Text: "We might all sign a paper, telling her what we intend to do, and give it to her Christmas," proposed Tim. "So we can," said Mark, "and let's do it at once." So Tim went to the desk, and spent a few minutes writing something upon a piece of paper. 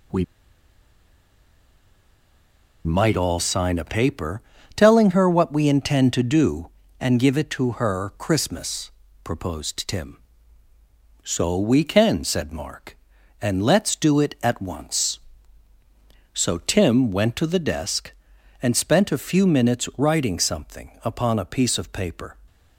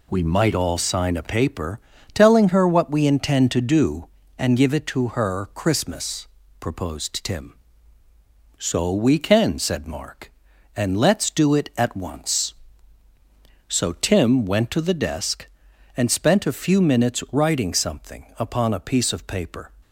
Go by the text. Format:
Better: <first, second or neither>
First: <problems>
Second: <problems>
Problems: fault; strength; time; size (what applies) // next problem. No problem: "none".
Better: second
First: pauses between "We" and "might"; strong; at 0.2 s; 2.6 s long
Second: none